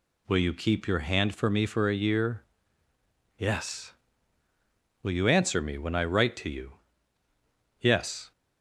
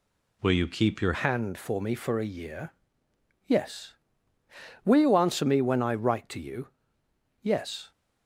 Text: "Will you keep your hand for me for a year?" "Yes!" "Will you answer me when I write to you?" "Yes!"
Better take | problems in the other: first | changes voice at "hand"; from 1.1 s on; 6.8 s long

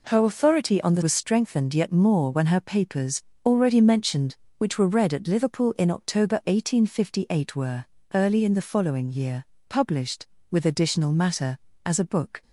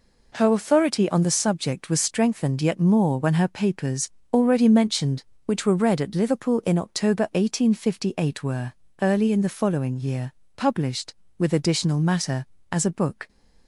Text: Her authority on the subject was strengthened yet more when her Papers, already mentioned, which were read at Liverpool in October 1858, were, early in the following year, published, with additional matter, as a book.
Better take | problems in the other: second | skips "subject"; at 1.0 s

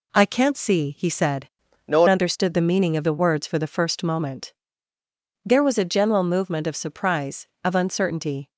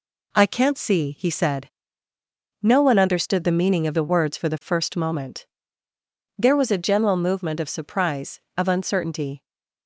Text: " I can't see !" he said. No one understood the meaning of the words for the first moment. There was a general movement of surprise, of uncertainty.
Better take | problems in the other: second | changes voice from "No" to "one"; from 1.8 to 2.0 s; 0.2 s long

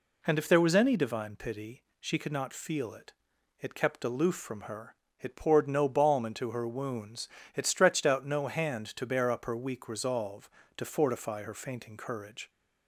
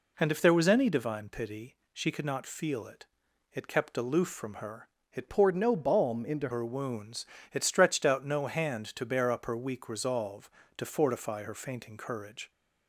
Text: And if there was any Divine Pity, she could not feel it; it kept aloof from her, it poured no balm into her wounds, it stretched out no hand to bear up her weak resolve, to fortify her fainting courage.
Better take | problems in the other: first | changes voice from "poured" to "into"; from 5.2 to 6.4 s; 1.2 s long

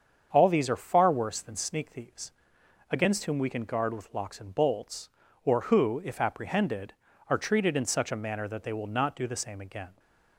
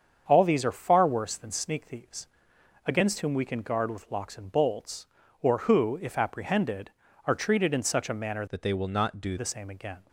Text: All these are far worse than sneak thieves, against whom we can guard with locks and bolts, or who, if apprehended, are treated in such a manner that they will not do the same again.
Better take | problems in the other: first | starts louder than the rest; strong; until 1.2 s; 7 dB; strong in the first // changes voice from "that" to "do"; from 8.4 to 9.3 s; 0.9 s long

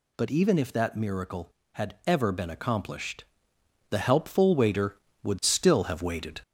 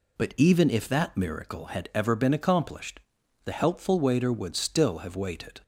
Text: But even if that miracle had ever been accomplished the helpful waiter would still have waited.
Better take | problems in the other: second | gets louder; throughout; 3.5 dB // pauses between "accomplished" and "the"; noticeable; at 3.2 s; 0.64 s long; also in the second

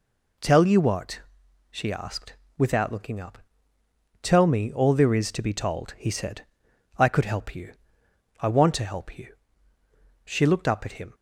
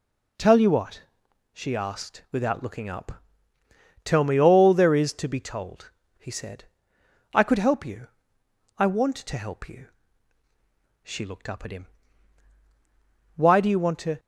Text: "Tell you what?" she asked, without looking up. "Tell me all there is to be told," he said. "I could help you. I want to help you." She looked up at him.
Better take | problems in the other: first | goes on to say "Why do you want to"; noticeable; from 13.3 s on; 0.82 s long

